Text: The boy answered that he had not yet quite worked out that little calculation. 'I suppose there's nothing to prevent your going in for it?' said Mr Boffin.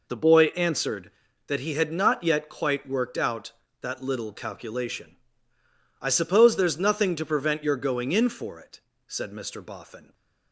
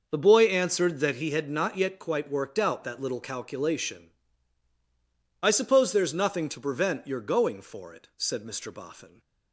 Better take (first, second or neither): first